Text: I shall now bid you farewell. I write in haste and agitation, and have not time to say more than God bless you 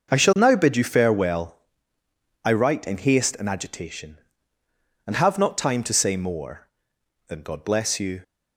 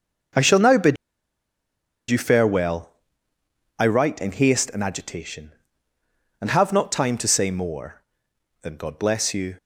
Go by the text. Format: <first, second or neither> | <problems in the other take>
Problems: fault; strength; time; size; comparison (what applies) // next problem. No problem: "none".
first | starts louder than the rest; noticeable; until 2.4 s; 6 dB; noticeable in the first // pauses between "bid" and "you"; at 0.9 s; 1.1 s long